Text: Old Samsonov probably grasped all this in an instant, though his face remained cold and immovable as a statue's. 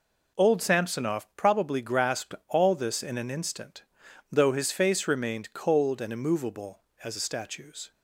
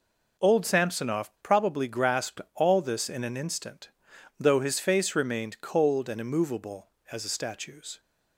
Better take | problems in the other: neither | none

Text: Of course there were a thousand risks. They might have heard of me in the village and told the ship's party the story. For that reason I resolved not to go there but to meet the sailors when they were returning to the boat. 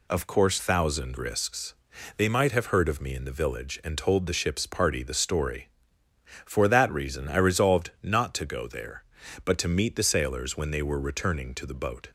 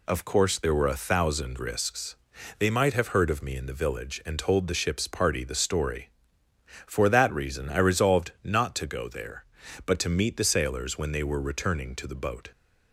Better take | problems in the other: second | skips "there were a"; at 0.5 s

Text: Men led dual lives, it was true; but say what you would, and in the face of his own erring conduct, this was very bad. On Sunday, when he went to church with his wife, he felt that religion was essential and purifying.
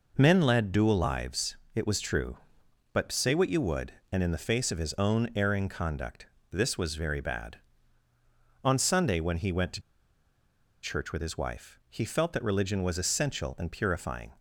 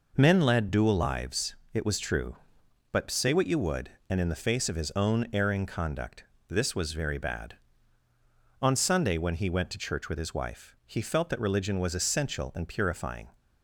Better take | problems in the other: second | pauses between "to" and "church"; at 9.8 s; 1.0 s long

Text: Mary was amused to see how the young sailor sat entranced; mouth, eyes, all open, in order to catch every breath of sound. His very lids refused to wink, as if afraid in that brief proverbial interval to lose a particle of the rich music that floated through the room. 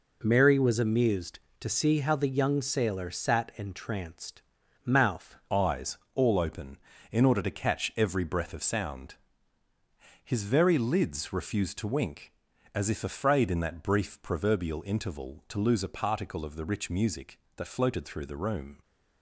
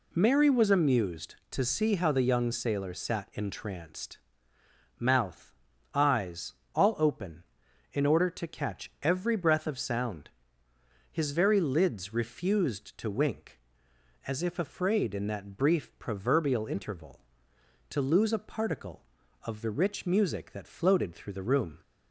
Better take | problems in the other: second | changes voice at "eyes"; from 5.4 s on; 13.4 s long

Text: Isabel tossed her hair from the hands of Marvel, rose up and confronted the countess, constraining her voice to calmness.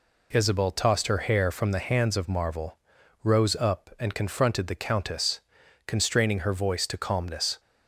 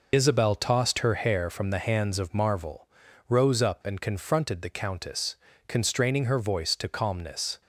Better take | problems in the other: first | loses the start of "Isabel"; at 0.1 s; 55 ms

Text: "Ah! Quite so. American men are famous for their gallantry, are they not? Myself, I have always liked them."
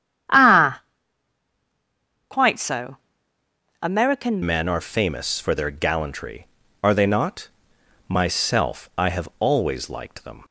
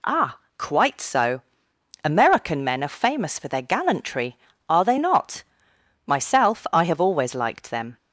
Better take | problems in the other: second | starts louder than the rest; strong; until 2.7 s; 9.5 dB // changes voice at "men"; from 4.4 s on; 6.0 s long

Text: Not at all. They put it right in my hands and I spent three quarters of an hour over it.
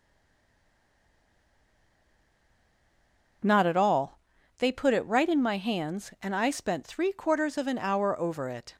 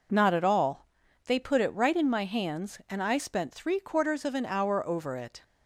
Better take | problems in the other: second | stays silent before the first word; strong; until 3.4 s; 3.4 s long

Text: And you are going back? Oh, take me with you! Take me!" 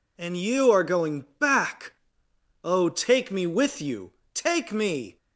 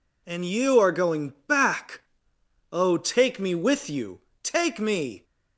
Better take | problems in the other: neither | none

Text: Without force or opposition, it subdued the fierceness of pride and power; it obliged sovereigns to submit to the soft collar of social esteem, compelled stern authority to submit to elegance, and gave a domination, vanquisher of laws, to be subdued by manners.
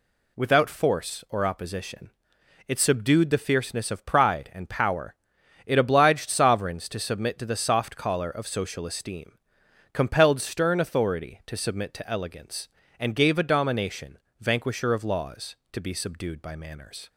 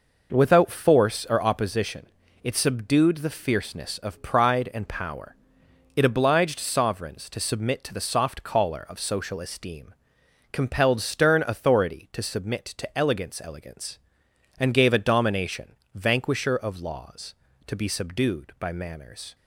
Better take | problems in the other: first | says "elegance" twice; at 13.4 s

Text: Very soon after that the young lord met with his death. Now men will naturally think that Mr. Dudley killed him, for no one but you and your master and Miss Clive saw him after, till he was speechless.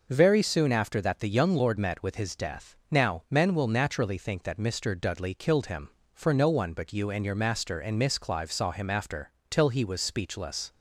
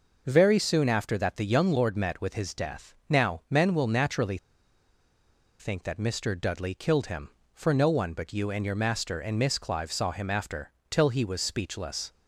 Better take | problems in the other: first | pauses between "naturally" and "think"; at 4.3 s; 1.2 s long

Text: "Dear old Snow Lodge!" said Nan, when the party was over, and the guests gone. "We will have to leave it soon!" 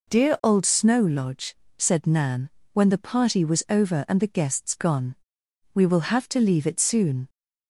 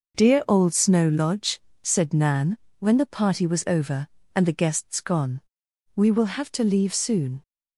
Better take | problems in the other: first | skips "it"; at 6.9 s

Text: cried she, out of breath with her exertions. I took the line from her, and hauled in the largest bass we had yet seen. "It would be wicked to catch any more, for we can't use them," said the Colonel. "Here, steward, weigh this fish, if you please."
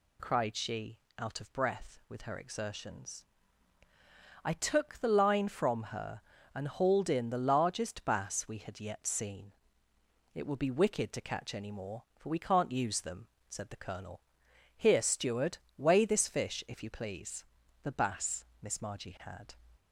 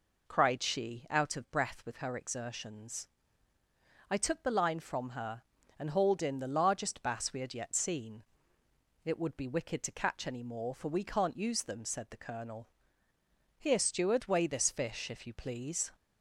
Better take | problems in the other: second | goes on to say "The bass Miss Margie had"; strong; from 17.8 s on; 1.7 s long

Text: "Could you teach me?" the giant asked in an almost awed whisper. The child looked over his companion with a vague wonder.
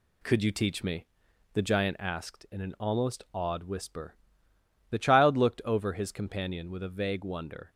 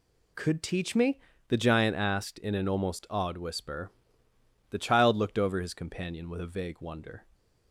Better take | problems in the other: first | skips "you"; at 0.6 s

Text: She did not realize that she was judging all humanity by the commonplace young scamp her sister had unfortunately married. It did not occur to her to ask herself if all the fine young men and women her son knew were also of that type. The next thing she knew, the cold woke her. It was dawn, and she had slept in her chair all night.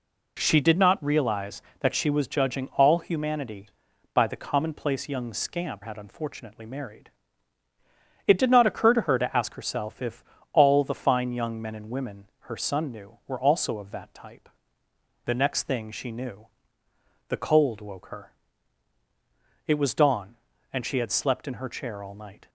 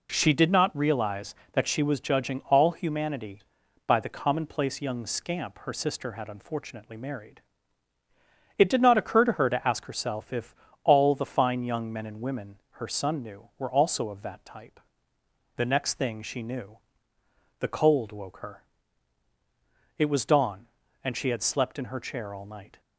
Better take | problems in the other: second | skips "her sister"; at 5.8 s // pauses between "if" and "all"; slight; at 10.2 s; 0.26 s long; slight in the second // pauses between "women" and "her"; slight; at 12.2 s; 0.16 s long; slight in the second

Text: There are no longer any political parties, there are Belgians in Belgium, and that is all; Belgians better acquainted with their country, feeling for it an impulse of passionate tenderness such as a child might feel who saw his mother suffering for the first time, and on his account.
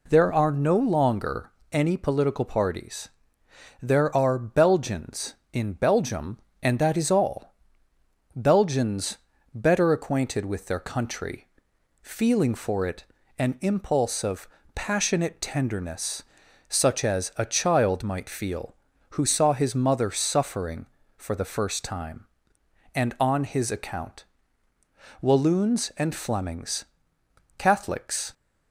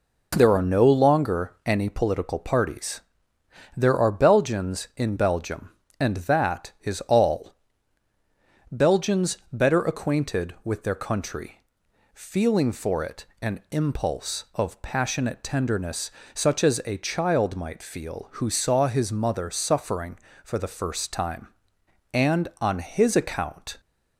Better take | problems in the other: second | pauses between "longer" and "any"; slight; at 1.5 s; 0.22 s long // pauses between "Belgians" and "better"; at 9.1 s; 0.38 s long; slight in the second // pauses between "it" and "an"; slight; at 13.0 s; 0.34 s long; slight in the second // pauses between "of" and "passionate"; slight; at 14.4 s; 0.28 s long // pauses between "tenderness" and "such"; noticeable; at 16.2 s; 0.46 s long; slight in the second // goes on to say "Walloons and Flemings Catholics"; strong; from 25.2 s on; 3.1 s long

